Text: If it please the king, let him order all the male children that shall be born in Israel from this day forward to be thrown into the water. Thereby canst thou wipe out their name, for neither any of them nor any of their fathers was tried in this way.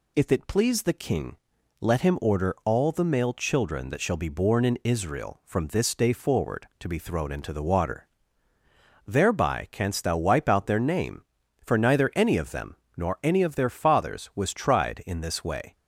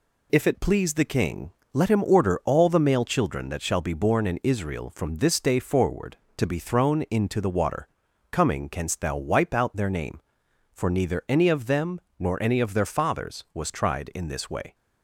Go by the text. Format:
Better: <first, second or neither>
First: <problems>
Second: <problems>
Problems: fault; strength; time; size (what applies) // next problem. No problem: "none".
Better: first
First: pauses between "them" and "nor"; slight; at 12.7 s; 0.20 s long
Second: says "Coming" for "Thereby"; at 8.3 s // pauses between "them" and "nor"; slight; at 11.9 s; 0.18 s long